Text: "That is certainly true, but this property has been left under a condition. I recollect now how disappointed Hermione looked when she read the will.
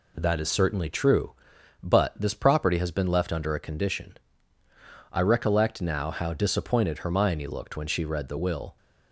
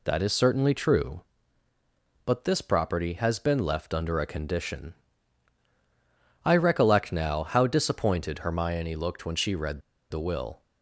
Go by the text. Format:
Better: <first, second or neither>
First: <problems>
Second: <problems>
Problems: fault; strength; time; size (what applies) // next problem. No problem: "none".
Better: first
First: none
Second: pauses between "read" and "the"; slight; at 9.8 s; 0.30 s long